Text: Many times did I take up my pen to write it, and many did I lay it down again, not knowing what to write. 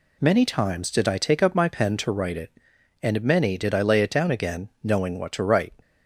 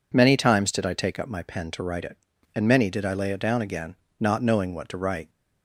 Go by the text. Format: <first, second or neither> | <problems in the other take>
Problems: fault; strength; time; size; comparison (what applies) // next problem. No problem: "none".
second | skips "not"; at 4.7 s